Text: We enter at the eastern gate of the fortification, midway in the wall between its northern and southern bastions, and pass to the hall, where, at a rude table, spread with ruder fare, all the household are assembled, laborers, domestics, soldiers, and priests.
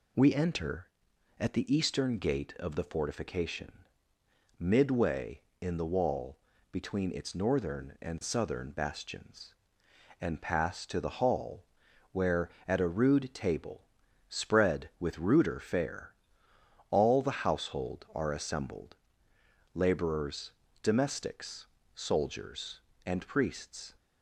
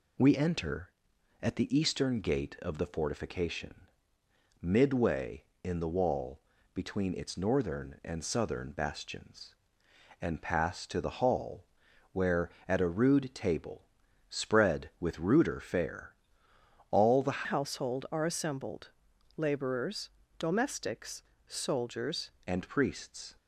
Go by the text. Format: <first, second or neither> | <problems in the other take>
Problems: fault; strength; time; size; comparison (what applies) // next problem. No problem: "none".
first | pauses between "wall" and "between"; slight; at 6.3 s; 0.34 s long; slight in the first // changes voice from "household" to "soldiers"; from 17.4 to 22.3 s; 4.9 s long